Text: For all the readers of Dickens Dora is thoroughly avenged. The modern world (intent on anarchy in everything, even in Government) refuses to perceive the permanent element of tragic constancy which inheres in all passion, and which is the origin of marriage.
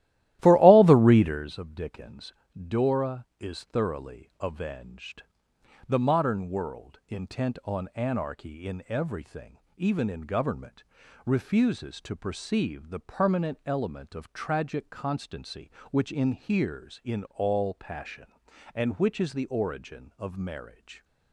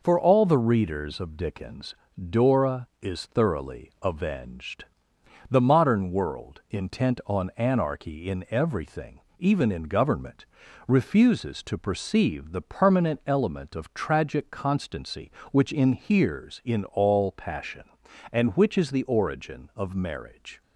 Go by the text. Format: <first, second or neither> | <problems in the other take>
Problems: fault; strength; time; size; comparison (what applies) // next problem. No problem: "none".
second | starts louder than the rest; strong; until 1.5 s; 14.5 dB // pauses between "Dickens" and "Dora"; slight; at 2.3 s; 0.24 s long; slight in the second